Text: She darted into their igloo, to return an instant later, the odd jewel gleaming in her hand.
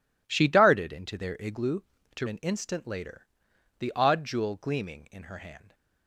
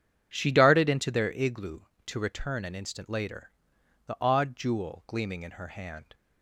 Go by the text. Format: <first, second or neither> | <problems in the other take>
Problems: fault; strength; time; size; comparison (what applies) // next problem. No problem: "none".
second | skips "return"; at 2.2 s